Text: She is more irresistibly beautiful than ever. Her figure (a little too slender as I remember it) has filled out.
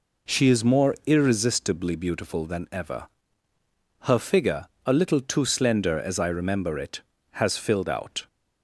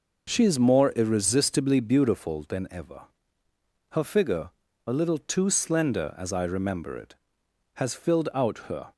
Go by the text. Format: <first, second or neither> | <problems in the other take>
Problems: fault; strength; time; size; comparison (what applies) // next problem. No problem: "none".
first | goes on to say "Her"; slight; from 8.6 s on; 0.24 s long